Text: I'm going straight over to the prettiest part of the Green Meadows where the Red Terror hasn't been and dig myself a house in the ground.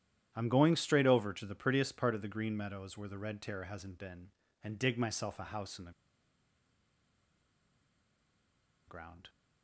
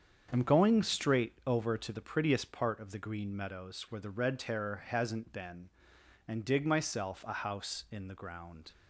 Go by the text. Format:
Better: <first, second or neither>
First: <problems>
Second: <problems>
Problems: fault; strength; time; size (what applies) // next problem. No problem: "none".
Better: second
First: starts louder than the rest; strong; until 1.3 s; 10.5 dB // pauses between "the" and "ground"; strong; at 5.9 s; 2.9 s long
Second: starts louder than the rest; strong; until 1.3 s; 7.5 dB